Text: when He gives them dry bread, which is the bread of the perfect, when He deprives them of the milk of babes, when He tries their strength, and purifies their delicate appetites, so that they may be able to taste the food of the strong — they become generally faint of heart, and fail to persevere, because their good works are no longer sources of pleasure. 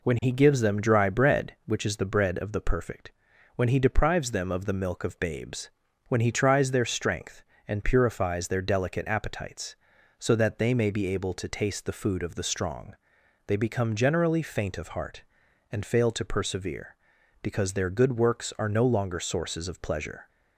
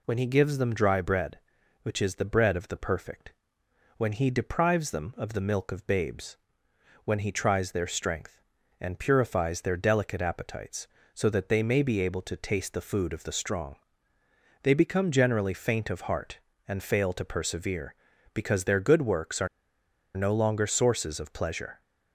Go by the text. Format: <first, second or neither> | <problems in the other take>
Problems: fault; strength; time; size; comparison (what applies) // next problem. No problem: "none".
first | pauses between "are" and "no"; noticeable; at 19.4 s; 0.69 s long